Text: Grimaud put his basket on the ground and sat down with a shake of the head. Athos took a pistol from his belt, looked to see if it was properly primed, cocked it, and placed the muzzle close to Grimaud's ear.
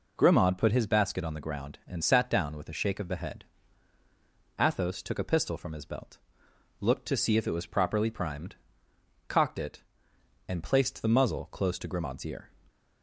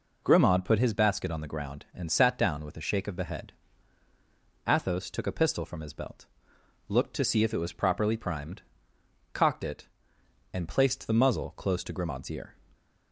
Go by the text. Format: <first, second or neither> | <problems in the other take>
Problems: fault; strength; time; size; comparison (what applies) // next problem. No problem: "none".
neither | none